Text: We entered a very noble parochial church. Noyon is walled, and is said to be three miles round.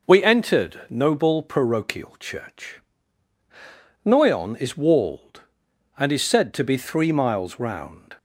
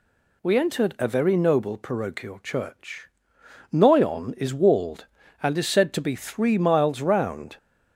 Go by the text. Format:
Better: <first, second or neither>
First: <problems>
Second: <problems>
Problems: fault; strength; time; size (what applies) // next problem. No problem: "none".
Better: second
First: skips "a very"; at 0.8 s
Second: none